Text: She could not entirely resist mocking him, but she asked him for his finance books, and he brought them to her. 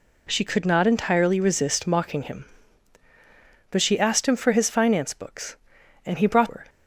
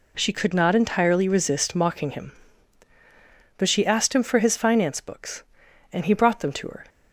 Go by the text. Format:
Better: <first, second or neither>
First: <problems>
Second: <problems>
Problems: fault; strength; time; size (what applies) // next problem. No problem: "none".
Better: second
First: skips "them to"; at 6.4 s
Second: none